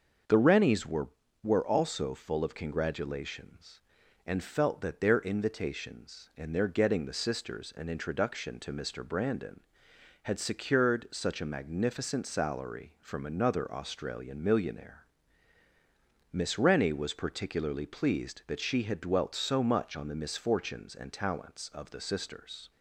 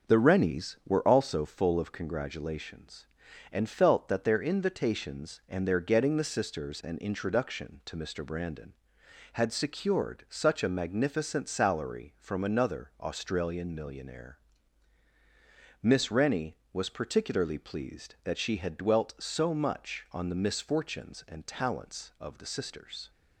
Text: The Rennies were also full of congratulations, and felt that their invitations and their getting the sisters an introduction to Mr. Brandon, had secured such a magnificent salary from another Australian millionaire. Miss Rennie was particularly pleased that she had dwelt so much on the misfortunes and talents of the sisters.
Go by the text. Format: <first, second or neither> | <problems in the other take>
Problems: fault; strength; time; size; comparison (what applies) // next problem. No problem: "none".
second | starts louder than the rest; until 1.6 s; 6.5 dB; also in the second // says "were" twice; at 1.4 s